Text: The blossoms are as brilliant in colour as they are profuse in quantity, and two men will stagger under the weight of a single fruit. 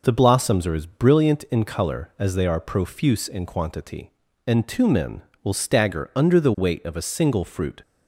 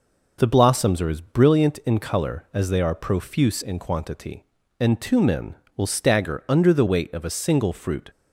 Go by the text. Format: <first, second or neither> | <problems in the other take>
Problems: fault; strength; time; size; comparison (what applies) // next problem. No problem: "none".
neither | none